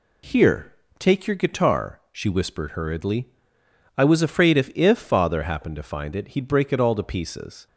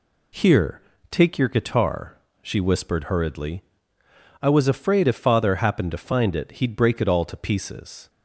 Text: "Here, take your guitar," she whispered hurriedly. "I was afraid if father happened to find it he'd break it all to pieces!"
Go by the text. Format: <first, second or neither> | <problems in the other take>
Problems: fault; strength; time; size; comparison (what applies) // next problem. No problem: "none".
second | says "if" twice; at 4.7 s